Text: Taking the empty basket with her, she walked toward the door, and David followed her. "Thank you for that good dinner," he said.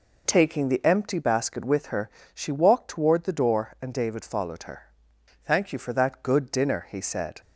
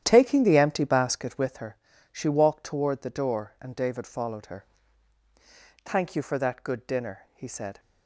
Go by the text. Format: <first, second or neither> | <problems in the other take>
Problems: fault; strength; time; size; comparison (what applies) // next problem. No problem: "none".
first | starts louder than the rest; strong; until 1.5 s; 11 dB